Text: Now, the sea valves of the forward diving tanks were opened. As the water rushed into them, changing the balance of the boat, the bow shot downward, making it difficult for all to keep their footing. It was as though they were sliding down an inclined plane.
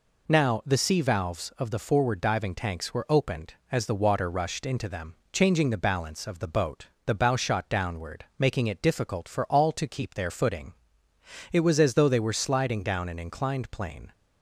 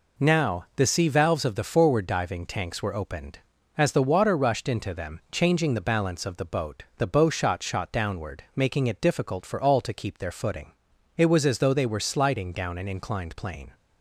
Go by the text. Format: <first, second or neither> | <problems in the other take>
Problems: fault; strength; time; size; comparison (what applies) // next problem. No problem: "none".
first | says "shot" twice; at 7.6 s